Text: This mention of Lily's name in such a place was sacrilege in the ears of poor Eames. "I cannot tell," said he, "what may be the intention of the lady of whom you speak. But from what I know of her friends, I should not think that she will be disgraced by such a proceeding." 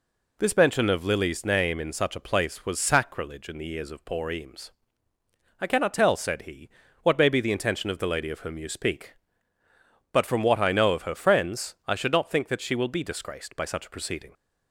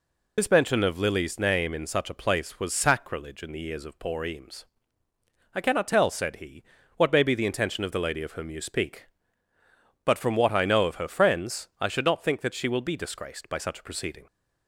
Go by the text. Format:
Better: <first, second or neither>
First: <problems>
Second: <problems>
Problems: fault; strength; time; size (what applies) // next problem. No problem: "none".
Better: first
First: none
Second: loses the start of "This"; at 0.3 s; 40 ms